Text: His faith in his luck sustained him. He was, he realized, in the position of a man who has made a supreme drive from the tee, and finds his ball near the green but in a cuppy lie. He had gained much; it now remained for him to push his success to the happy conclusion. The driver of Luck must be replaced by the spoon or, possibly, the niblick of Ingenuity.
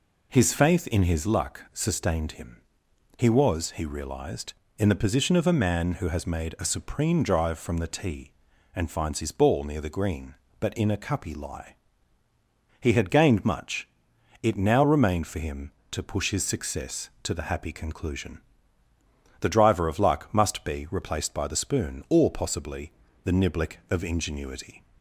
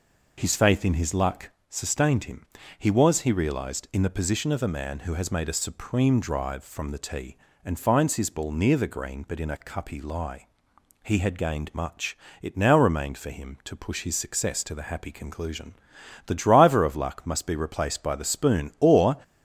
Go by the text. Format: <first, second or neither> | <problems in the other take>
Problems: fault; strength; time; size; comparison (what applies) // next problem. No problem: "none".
first | pauses between "luck" and "sustained"; slight; at 1.5 s; 0.18 s long // stops before "possibly the niblick of Ingenuity"; at 19.2 s